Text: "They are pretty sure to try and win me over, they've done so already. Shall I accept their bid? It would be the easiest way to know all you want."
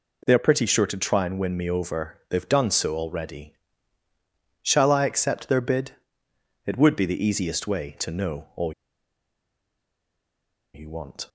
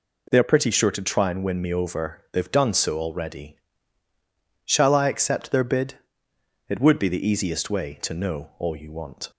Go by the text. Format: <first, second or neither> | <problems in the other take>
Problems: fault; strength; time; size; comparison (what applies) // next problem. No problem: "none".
second | pauses between "all" and "you"; strong; at 8.7 s; 2.0 s long